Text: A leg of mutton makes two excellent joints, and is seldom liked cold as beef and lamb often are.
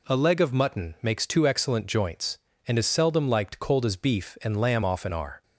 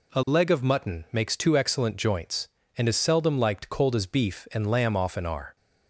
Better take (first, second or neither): neither